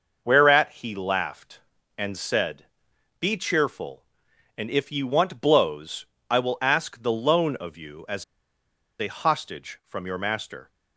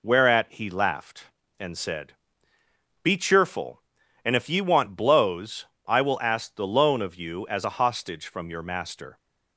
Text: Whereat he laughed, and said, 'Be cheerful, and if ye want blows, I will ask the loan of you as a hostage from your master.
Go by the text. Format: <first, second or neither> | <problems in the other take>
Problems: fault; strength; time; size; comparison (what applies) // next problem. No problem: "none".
second | starts louder than the rest; noticeable; until 1.2 s; 6 dB // pauses between "as" and "a"; noticeable; at 8.2 s; 0.75 s long